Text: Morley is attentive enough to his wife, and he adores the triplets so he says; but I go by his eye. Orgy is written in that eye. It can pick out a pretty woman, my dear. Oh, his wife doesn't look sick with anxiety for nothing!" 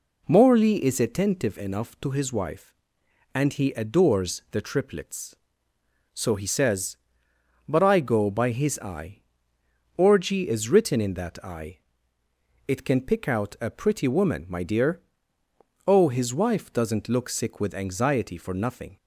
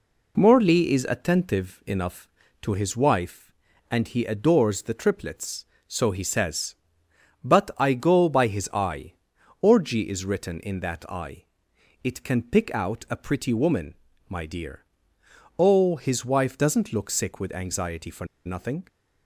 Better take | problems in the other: first | pauses between "for" and "nothing"; slight; at 18.2 s; 0.19 s long

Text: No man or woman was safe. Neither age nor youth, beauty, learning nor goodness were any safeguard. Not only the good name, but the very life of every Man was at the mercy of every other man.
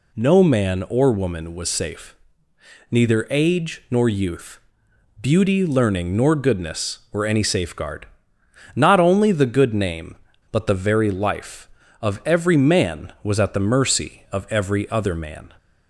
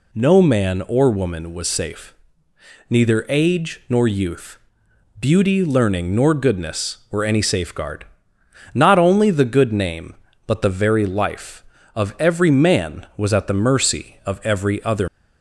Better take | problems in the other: first | stops before "man"; at 15.0 s

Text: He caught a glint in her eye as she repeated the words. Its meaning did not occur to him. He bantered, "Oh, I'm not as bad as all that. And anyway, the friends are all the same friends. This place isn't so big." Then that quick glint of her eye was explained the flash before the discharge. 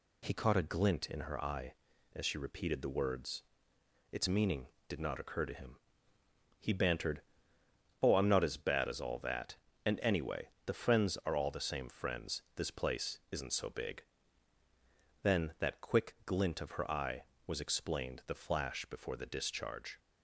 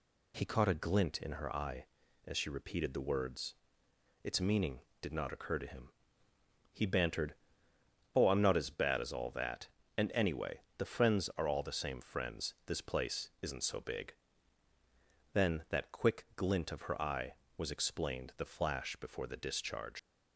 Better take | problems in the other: first | leaves "discharge" unfinished; at 19.9 s; 95 ms

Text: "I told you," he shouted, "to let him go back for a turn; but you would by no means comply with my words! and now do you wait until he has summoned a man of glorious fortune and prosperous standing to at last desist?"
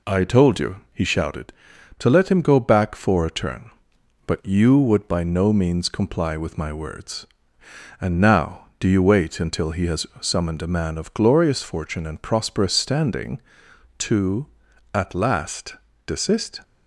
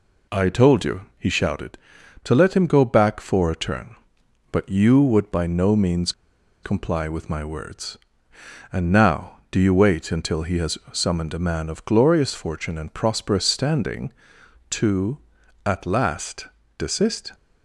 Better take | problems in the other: first | pauses between "means" and "comply"; noticeable; at 6.1 s; 0.51 s long // pauses between "has" and "summoned"; slight; at 10.7 s; 0.16 s long; slight in the first // pauses between "last" and "desist"; slight; at 16.4 s; 0.30 s long; slight in the first

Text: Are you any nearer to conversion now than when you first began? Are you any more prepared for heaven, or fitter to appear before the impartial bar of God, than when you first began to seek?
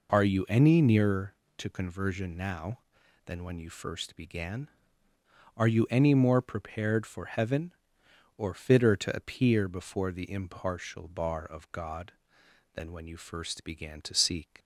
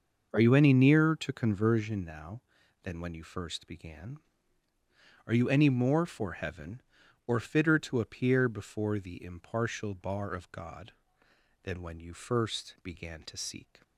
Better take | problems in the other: first | starts louder than the rest; noticeable; until 1.3 s; 6 dB // skips "prepared"; at 6.0 s

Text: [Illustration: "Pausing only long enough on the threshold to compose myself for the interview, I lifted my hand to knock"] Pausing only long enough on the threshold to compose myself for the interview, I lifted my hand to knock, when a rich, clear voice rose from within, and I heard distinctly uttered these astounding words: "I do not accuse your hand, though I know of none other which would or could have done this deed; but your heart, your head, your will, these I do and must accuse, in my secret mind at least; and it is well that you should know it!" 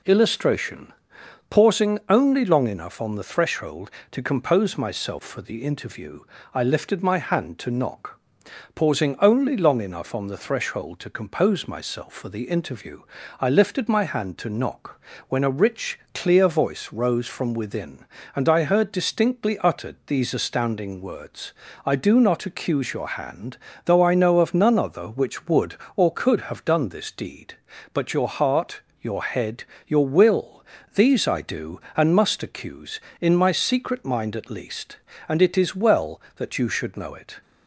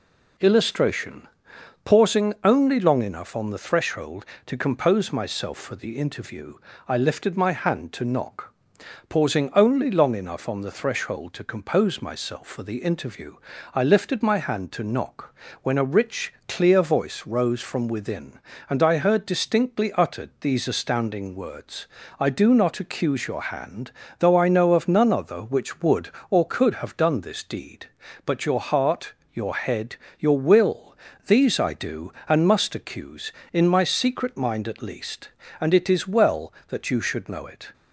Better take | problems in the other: neither | pauses between "knock" and "Pausing"; noticeable; the same in both

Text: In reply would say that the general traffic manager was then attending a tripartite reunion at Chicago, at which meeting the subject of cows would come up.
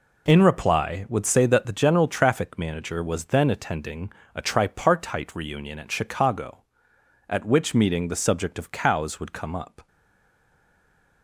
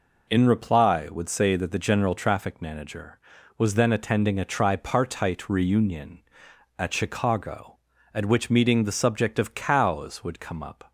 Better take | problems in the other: second | pauses between "attending" and "a"; slight; at 4.1 s; 0.24 s long // stays silent after the last word; noticeable; from 9.8 s on; 1.4 s long

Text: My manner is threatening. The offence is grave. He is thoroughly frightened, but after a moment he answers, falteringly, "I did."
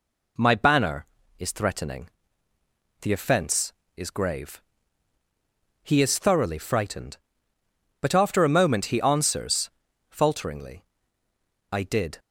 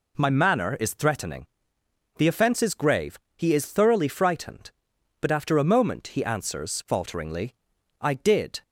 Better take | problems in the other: second | says "banner" for "manner"; at 0.5 s

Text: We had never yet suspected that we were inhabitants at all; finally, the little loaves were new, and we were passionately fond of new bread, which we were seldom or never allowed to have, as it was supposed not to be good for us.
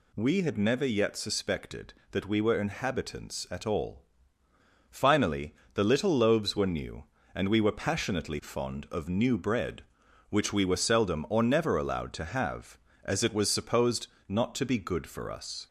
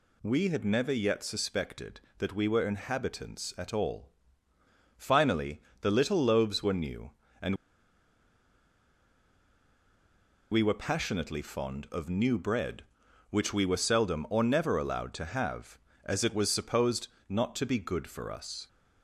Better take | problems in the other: first | pauses between "and" and "we"; strong; at 7.5 s; 2.9 s long // pauses between "supposed" and "not"; slight; at 17.0 s; 0.22 s long; slight in the first

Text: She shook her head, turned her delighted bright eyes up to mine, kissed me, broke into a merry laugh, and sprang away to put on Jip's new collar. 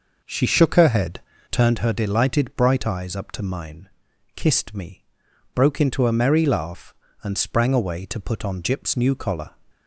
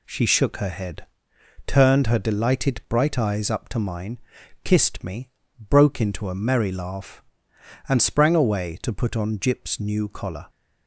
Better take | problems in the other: second | starts louder than the rest; noticeable; until 1.7 s; 5.5 dB

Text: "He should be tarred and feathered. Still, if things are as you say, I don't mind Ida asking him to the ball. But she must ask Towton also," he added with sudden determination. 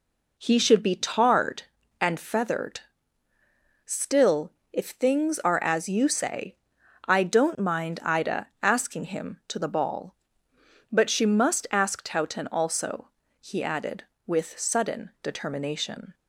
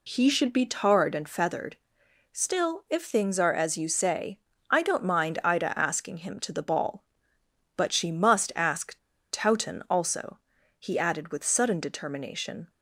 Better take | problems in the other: first | pauses between "ask" and "Towton"; at 8.9 s; 0.36 s long

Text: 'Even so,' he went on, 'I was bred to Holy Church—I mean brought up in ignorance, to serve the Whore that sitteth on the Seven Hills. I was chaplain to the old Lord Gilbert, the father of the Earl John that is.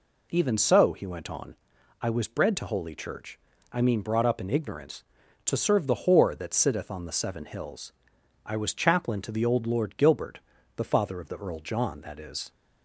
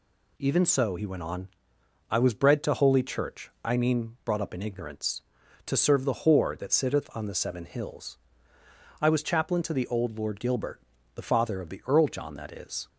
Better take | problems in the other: neither | none

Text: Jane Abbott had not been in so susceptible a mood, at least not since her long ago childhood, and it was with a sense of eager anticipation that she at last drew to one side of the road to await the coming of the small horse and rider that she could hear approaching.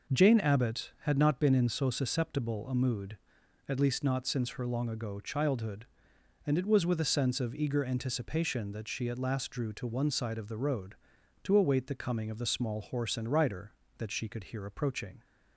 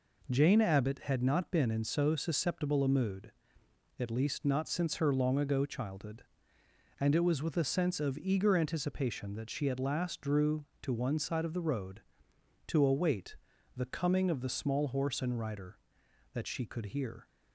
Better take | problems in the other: first | pauses between "await" and "the"; at 13.3 s; 0.42 s long // stops before "approaching"; at 17.2 s

